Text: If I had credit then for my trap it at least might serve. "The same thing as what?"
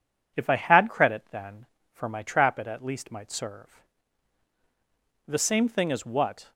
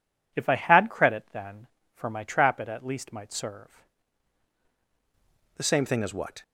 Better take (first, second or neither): first